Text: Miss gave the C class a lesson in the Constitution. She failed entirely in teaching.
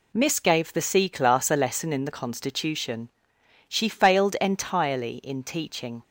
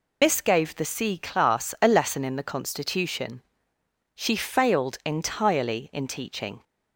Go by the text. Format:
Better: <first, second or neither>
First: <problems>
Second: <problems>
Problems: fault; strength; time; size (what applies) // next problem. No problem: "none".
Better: first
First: none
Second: loses the start of "Miss"; at 0.2 s; 65 ms